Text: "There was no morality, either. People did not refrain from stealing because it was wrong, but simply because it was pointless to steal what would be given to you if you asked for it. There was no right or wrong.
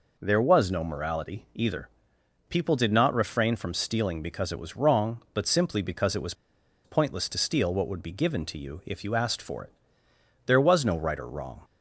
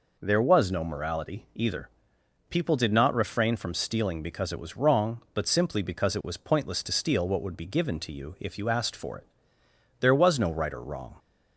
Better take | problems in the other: second | pauses between "was" and "pointless"; noticeable; at 6.3 s; 0.51 s long

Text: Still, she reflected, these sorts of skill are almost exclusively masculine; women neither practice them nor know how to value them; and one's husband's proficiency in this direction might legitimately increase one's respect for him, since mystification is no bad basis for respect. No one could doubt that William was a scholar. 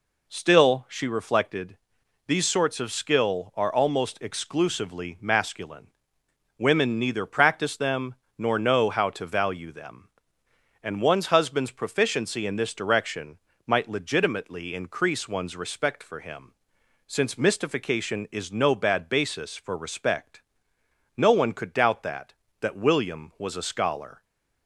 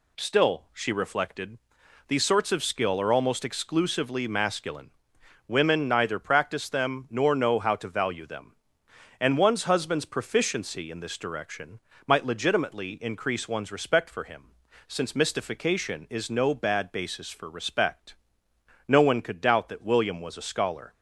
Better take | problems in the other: second | pauses between "them" and "nor"; slight; at 8.1 s; 0.24 s long // pauses between "direction" and "might"; slight; at 13.3 s; 0.30 s long; slight in the second // says "that" twice; at 22.6 s // stays silent after the last word; slight; from 24.1 s on; 0.5 s long

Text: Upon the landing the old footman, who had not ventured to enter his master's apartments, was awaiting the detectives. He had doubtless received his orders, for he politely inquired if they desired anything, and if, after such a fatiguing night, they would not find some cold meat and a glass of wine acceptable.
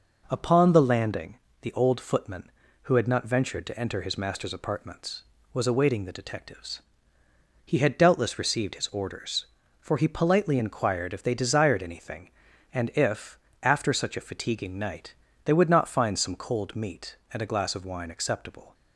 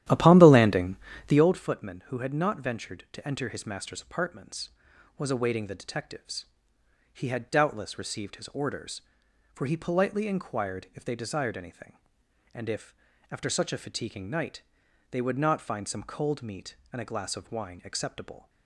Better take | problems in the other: first | starts louder than the rest; strong; until 1.5 s; 12 dB // pauses between "landing" and "the"; slight; at 0.9 s; 0.32 s long; slight in the first

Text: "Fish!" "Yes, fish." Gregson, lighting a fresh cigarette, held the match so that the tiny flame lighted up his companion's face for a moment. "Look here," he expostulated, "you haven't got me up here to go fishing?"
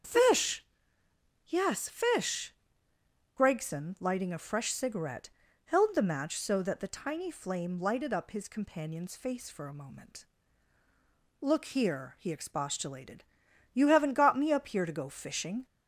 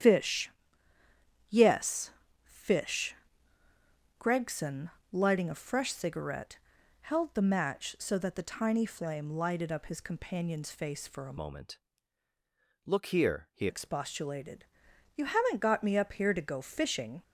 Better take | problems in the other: first | starts louder than the rest; strong; until 2.0 s; 9.5 dB; strong in the first // changes voice from "moment" to "he"; from 11.3 to 13.6 s; 2.3 s long

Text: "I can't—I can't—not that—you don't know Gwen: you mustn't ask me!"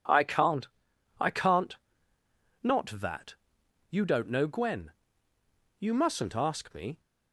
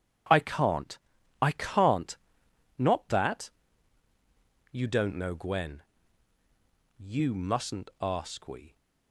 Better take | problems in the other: first | says "we" for "me"; at 8.4 s

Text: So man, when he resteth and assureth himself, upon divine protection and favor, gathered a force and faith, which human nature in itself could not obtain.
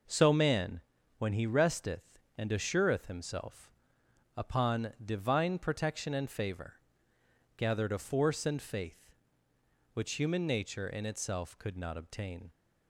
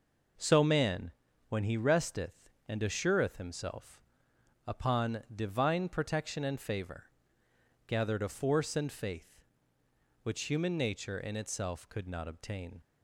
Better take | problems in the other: neither | none

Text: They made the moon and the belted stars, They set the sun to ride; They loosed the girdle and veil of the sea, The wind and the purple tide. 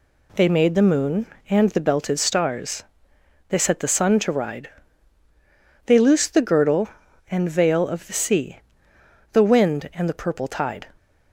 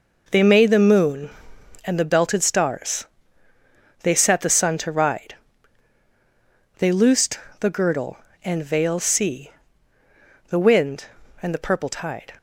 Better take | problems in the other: first | pauses between "loosed" and "the"; slight; at 7.3 s; 0.22 s long // skips "of the"; at 8.9 s

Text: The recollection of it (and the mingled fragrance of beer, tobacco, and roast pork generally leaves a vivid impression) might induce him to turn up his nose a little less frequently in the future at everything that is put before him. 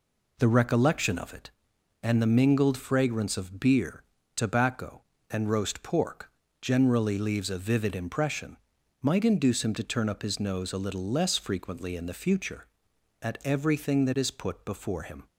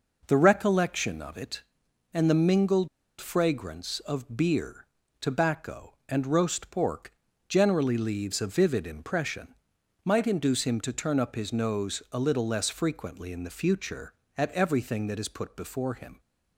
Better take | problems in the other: first | pauses between "mingled" and "fragrance"; slight; at 2.8 s; 0.31 s long // pauses between "pork" and "generally"; slight; at 7.1 s; 0.36 s long; slight in the first

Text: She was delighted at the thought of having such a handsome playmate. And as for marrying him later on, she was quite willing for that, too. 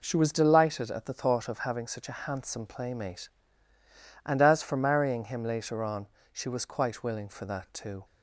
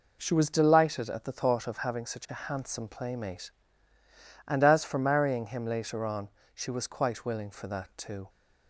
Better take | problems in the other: neither | none

